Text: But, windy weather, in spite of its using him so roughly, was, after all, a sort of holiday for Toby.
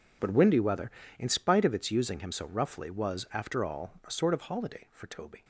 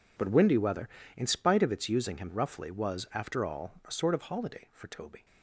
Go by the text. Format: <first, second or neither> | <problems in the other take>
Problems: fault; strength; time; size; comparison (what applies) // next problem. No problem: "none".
first | skips "so"; at 2.2 s